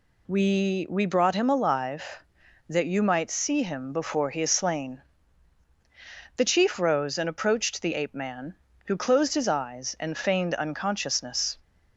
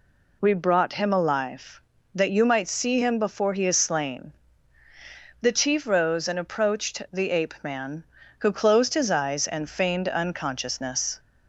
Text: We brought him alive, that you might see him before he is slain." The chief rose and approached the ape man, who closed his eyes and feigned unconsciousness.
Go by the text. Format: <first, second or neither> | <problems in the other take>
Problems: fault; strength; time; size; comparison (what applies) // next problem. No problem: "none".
second | says "We" twice; at 0.8 s